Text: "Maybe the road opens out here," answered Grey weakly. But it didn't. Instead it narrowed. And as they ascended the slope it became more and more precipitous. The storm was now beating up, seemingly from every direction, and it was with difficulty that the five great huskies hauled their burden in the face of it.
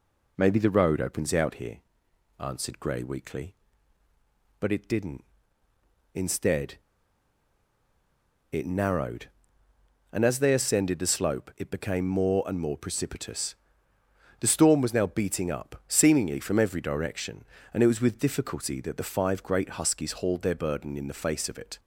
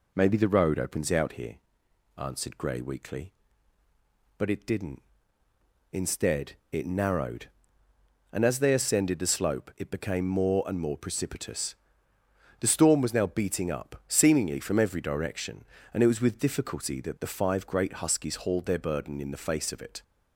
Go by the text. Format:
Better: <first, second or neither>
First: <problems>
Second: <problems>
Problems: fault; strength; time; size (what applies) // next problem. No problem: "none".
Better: second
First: pauses between "Instead" and "it"; strong; at 6.7 s; 1.7 s long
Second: none